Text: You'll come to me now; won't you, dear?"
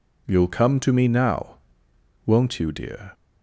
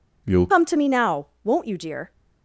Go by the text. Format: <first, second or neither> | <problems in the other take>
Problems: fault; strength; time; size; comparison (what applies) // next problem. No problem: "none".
first | changes voice at "come"; from 0.5 s on; 1.6 s long